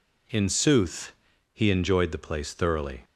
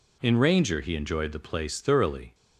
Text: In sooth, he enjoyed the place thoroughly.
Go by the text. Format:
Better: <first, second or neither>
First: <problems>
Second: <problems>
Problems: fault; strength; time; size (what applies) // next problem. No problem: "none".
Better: first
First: none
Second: says "ranger" for "sooth"; at 0.3 s